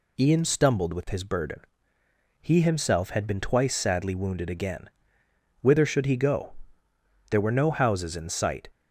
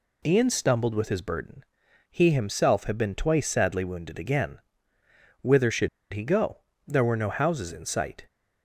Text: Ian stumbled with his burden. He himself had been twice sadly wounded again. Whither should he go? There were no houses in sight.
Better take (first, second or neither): first